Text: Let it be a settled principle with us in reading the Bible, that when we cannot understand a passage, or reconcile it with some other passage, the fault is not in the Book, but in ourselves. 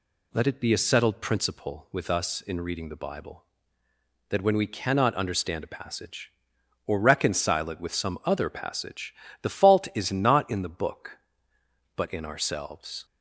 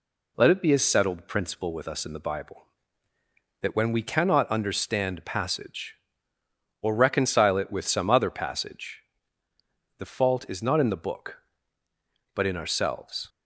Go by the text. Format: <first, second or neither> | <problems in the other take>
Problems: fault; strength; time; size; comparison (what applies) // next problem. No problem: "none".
first | skips "reading"; at 2.1 s